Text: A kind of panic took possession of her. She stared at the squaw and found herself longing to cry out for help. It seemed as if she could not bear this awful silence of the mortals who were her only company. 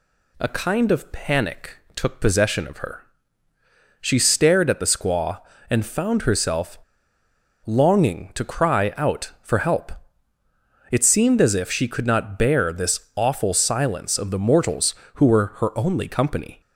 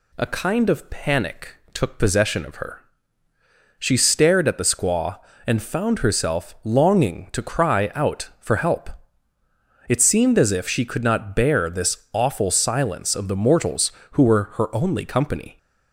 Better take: second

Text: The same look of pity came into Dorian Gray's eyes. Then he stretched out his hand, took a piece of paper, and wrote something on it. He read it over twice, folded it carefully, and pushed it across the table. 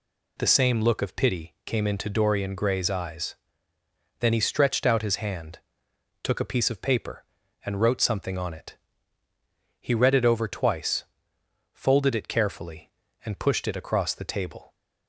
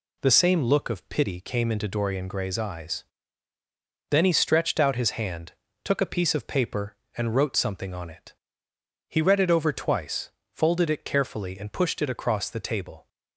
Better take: neither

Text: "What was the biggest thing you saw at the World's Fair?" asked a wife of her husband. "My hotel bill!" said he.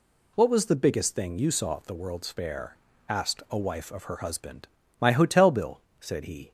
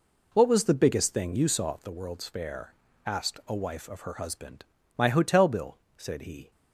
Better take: first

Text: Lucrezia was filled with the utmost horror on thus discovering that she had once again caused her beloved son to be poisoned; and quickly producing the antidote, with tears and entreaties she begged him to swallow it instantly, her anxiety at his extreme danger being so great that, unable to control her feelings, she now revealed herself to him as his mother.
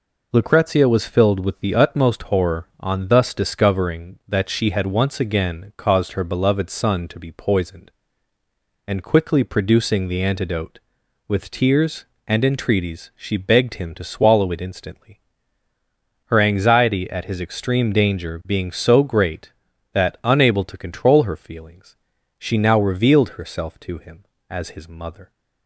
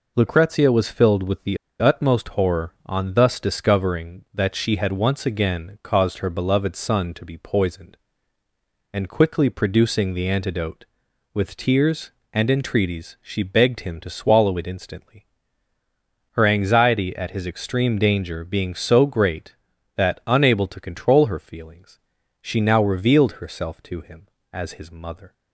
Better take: first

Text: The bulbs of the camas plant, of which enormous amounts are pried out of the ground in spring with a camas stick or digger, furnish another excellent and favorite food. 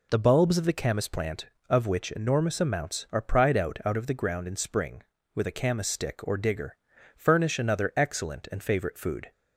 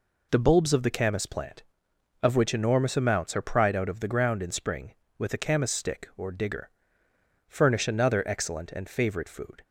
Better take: second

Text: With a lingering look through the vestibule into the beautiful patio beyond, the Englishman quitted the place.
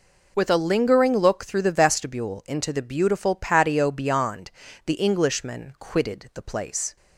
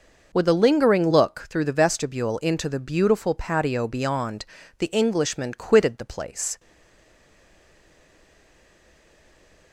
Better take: first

